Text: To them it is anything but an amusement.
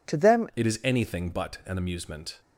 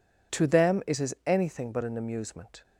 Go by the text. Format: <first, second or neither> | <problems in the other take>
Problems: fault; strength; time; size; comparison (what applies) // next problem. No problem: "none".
second | changes voice at "it"; from 0.5 s on; 1.9 s long